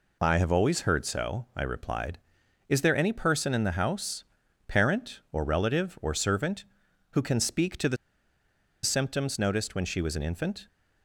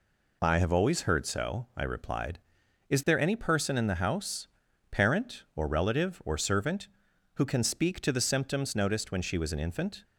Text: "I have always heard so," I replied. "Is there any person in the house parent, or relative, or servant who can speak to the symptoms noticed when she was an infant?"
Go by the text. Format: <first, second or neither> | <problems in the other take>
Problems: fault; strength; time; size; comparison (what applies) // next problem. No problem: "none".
second | pauses between "house" and "parent"; at 4.2 s; 0.42 s long; also in the second // pauses between "the" and "symptoms"; noticeable; at 7.9 s; 0.86 s long